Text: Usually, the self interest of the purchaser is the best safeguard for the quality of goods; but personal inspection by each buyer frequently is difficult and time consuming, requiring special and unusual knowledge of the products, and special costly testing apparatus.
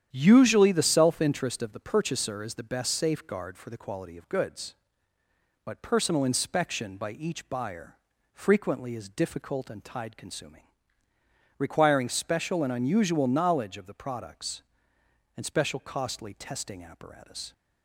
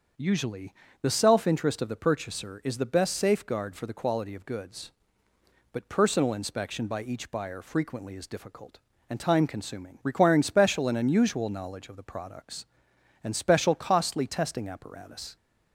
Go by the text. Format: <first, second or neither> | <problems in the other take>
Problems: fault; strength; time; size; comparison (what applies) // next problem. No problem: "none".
second | starts louder than the rest; strong; until 1.1 s; 10 dB; also in the second // pauses between "buyer" and "frequently"; slight; at 7.9 s; 0.36 s long // says "tide" for "time"; at 9.8 s